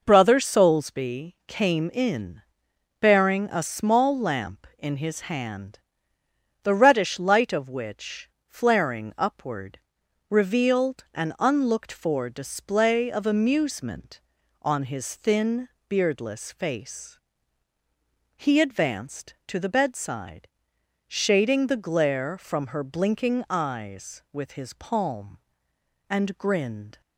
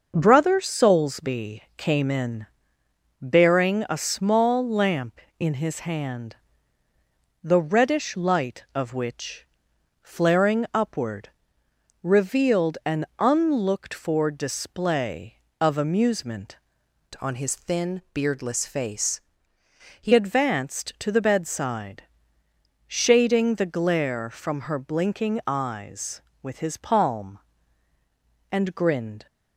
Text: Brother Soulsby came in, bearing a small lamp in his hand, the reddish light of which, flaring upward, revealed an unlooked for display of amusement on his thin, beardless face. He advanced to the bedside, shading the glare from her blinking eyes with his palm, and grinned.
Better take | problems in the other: first | starts louder than the rest; noticeable; until 1.1 s; 6 dB // changes voice from "on" to "He"; from 17.2 to 20.1 s; 2.9 s long

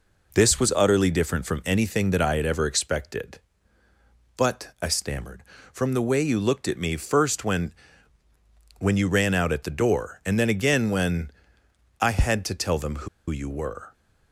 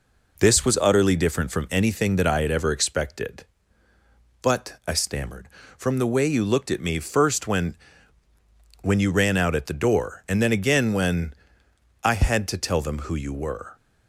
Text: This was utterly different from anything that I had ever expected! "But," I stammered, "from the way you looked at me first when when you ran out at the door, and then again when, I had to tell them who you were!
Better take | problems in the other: second | pauses between "when" and "when"; at 7.7 s; 1.0 s long; also in the second // pauses between "who" and "you"; slight; at 13.0 s; 0.21 s long

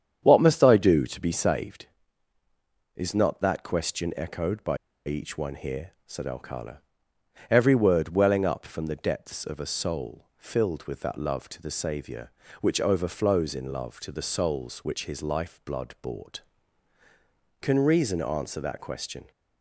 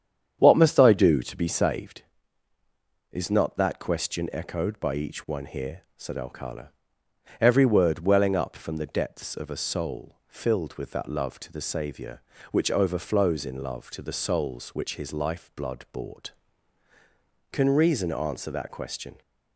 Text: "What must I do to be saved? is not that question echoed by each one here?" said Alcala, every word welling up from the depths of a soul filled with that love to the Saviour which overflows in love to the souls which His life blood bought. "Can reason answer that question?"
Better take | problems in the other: second | starts louder than the rest; strong; until 1.2 s; 8.5 dB; strong in the second // pauses between "by" and "each"; slight; at 4.7 s; 0.29 s long

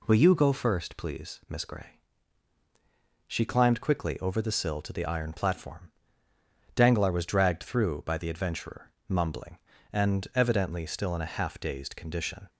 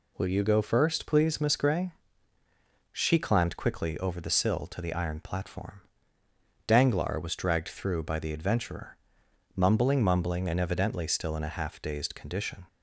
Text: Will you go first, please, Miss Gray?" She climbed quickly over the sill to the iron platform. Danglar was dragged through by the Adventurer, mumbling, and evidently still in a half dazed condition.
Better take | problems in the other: first | says "mumbling" twice; at 10.0 s

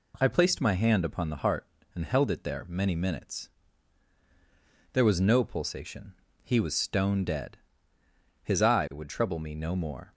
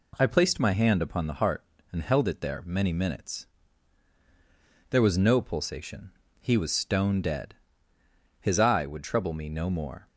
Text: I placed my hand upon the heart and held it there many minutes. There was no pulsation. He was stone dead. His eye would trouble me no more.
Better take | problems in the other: neither | none

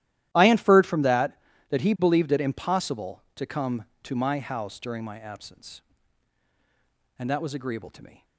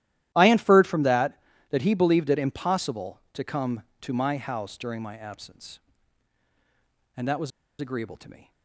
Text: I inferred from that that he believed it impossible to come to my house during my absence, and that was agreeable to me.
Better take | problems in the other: first | starts louder than the rest; strong; until 1.3 s; 13.5 dB; strong in the first // pauses between "was" and "agreeable"; slight; at 7.5 s; 0.30 s long

